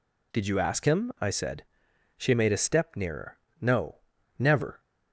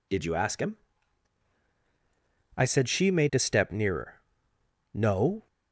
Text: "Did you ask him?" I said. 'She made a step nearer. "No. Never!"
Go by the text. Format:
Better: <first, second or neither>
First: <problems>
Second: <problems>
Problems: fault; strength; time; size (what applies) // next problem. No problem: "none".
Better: first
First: none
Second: stops before "Never"; at 5.4 s